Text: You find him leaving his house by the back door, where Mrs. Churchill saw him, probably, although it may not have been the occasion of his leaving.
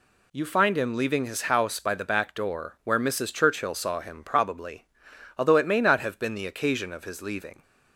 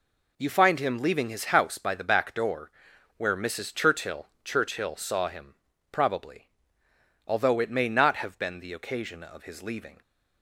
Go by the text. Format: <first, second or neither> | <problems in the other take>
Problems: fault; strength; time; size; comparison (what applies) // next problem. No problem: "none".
first | says "Churchill" twice; at 4.4 s